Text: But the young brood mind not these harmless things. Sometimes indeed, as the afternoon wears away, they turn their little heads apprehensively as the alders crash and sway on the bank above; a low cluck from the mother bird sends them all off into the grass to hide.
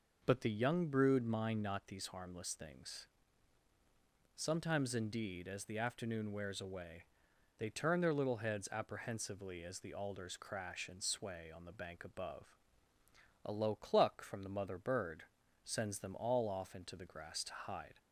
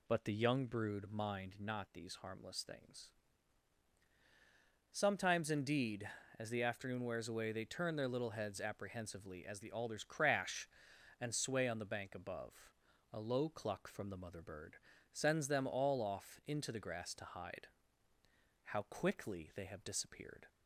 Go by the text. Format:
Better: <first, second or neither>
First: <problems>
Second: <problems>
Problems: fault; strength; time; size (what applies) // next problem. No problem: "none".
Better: first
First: pauses between "bird" and "sends"; at 15.2 s; 0.40 s long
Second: pauses between "bird" and "sends"; slight; at 14.7 s; 0.34 s long // goes on to say "How quickly they have disappeared"; strong; from 18.6 s on; 1.8 s long